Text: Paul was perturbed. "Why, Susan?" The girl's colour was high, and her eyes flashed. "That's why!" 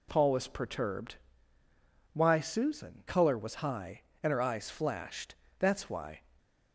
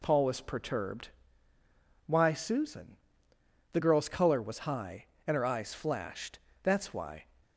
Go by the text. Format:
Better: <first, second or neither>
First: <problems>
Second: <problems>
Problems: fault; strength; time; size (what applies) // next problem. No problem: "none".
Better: second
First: skips "The girl's"; at 3.0 s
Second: none